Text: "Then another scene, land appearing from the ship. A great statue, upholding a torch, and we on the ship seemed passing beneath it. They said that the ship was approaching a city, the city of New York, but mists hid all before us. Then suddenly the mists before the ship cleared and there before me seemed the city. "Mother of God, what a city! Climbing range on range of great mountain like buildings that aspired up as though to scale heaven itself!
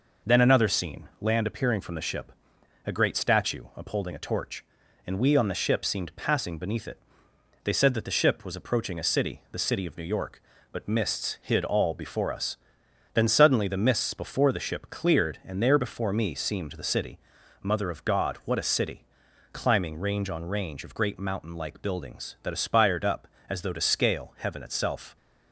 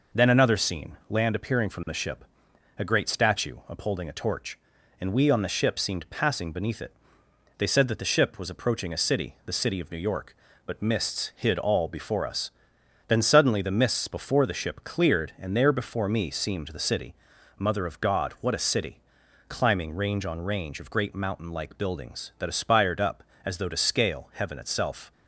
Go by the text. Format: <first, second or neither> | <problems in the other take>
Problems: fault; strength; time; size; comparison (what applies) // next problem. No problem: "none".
neither | none